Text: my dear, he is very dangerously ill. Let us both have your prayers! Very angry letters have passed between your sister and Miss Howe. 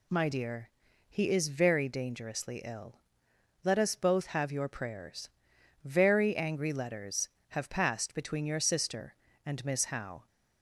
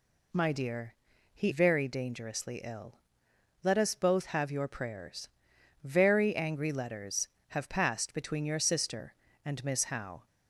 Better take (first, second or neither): first